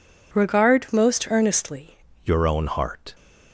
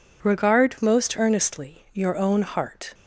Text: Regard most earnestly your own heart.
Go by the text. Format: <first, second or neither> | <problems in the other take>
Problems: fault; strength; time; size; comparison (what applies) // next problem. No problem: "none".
second | changes voice at "your"; from 2.2 s on; 0.9 s long